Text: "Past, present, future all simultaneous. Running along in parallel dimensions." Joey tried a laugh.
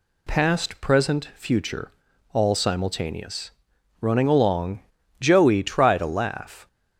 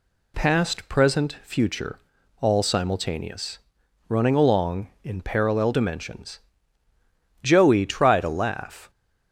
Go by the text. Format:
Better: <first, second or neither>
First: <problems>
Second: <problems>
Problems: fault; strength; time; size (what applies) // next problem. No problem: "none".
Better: second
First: pauses between "future" and "all"; at 1.8 s; 0.44 s long // skips "in parallel dimensions"; at 5.0 s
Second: pauses between "future" and "all"; at 1.9 s; 0.44 s long